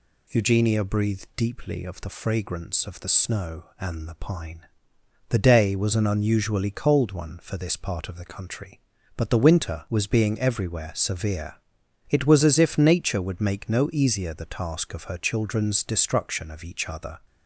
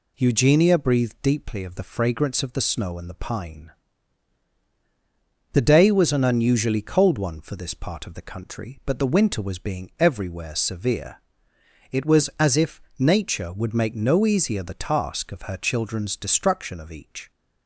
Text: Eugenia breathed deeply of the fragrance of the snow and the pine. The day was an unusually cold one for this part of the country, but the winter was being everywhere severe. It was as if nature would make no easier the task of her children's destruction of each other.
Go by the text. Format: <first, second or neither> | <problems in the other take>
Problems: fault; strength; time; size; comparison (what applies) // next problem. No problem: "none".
first | pauses between "if" and "nature"; slight; at 12.8 s; 0.16 s long // stops before "other"; at 17.3 s